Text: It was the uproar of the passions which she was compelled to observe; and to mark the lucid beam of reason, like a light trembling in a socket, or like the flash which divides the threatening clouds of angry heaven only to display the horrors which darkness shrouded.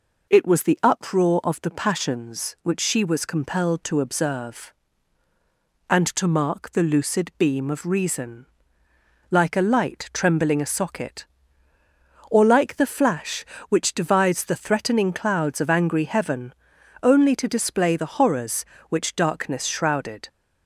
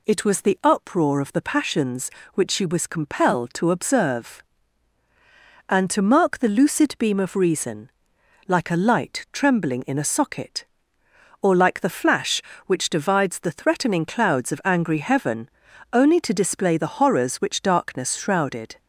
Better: second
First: skips "in"; at 10.5 s // pauses between "heaven" and "only"; noticeable; at 16.5 s; 0.48 s long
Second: pauses between "heaven" and "only"; at 15.4 s; 0.42 s long

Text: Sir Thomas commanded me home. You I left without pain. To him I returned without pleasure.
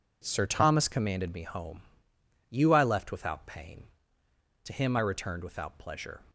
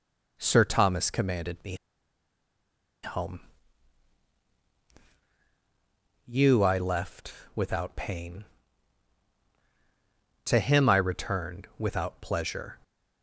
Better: first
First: none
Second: pauses between "me" and "home"; strong; at 1.7 s; 1.2 s long // pauses between "left" and "without"; slight; at 7.3 s; 0.22 s long

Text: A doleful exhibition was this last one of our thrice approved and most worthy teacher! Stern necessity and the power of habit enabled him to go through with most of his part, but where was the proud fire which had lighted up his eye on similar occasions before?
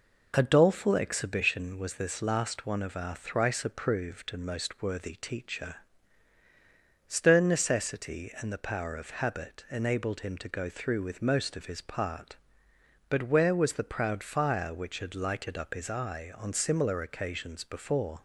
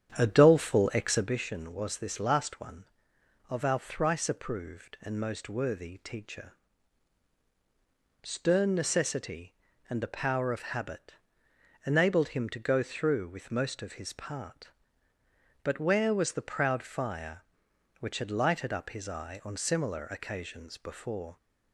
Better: first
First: none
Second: starts louder than the rest; strong; until 1.4 s; 9 dB // pauses between "habit" and "enabled"; noticeable; at 11.1 s; 0.74 s long

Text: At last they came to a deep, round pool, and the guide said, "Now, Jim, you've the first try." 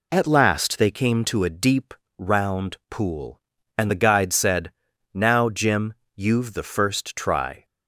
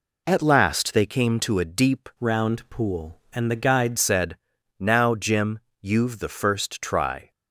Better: first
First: none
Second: changes voice from "round" to "guide"; from 2.2 to 3.9 s; 1.7 s long

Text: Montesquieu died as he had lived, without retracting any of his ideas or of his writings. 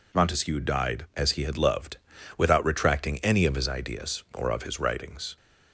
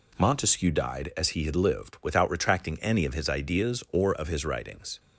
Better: second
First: says "loved" for "lived"; at 1.5 s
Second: none

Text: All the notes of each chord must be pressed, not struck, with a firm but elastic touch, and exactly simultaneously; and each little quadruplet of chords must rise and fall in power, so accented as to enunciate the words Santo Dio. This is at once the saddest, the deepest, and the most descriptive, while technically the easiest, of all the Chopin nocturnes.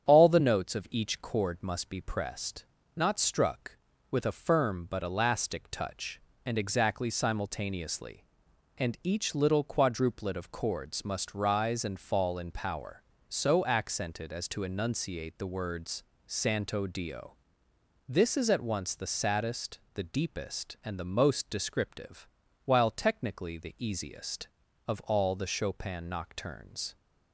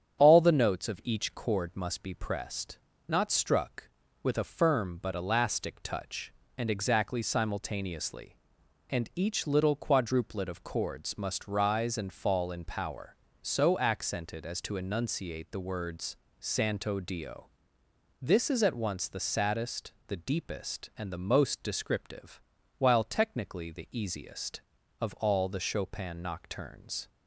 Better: neither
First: starts louder than the rest; strong; until 1.1 s; 8.5 dB // pauses between "words" and "Santo"; slight; at 16.0 s; 0.24 s long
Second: starts louder than the rest; strong; until 1.2 s; 8.5 dB // pauses between "words" and "Santo"; slight; at 16.1 s; 0.24 s long

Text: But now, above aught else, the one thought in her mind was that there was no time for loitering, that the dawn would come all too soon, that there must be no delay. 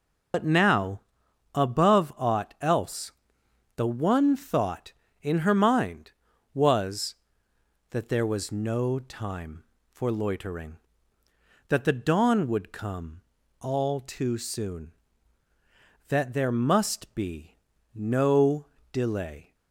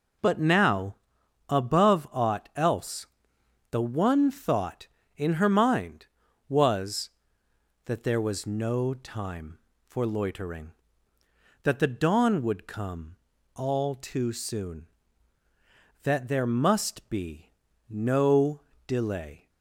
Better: second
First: loses the start of "But"; at 0.3 s; 80 ms // pauses between "come" and "all"; at 13.2 s; 0.40 s long // pauses between "be" and "no"; at 17.5 s; 0.38 s long // pauses between "no" and "delay"; slight; at 18.6 s; 0.26 s long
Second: pauses between "come" and "all"; at 13.1 s; 0.40 s long // pauses between "be" and "no"; at 17.5 s; 0.38 s long // pauses between "no" and "delay"; slight; at 18.6 s; 0.26 s long

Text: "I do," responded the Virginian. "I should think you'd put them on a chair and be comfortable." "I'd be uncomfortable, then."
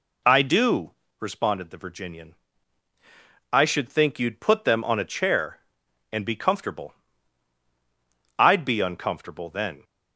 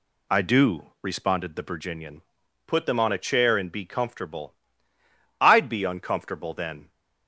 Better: first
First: none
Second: skips "I should think you'd"; at 2.4 s

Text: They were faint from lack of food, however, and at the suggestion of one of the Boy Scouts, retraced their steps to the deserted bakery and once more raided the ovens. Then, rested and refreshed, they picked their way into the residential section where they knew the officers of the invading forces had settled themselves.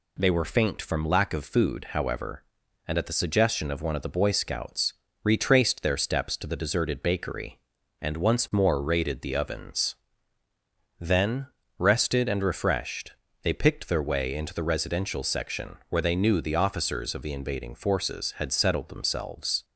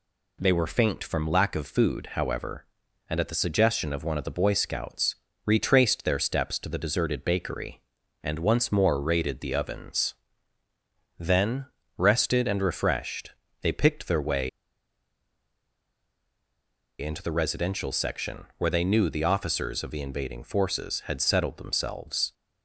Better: first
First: none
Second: pauses between "way" and "into"; strong; at 14.4 s; 2.5 s long

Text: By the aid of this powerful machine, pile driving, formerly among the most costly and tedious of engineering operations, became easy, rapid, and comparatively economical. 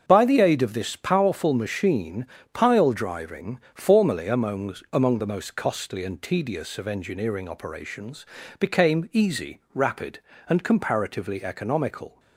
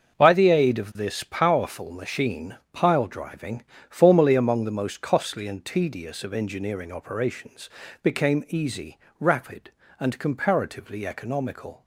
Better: second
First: starts louder than the rest; until 1.0 s; 7 dB // says "among" twice; at 4.9 s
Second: starts louder than the rest; until 1.2 s; 6.5 dB

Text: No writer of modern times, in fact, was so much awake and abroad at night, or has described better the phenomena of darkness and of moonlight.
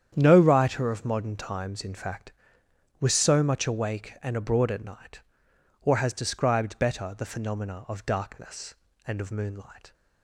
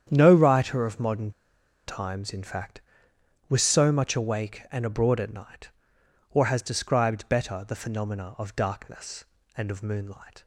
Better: first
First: starts louder than the rest; strong; until 1.1 s; 9 dB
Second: starts louder than the rest; strong; until 1.1 s; 9 dB // pauses between "modern" and "times"; noticeable; at 1.2 s; 0.57 s long

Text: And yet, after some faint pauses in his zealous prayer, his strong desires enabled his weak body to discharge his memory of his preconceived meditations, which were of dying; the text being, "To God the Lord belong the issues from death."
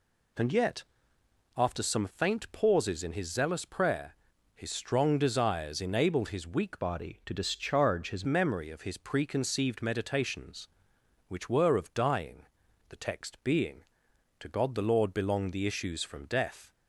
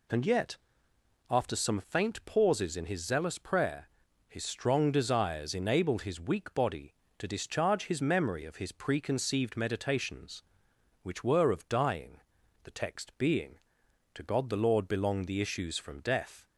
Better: second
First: changes voice from "body" to "his"; from 6.8 to 8.2 s; 1.4 s long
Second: none

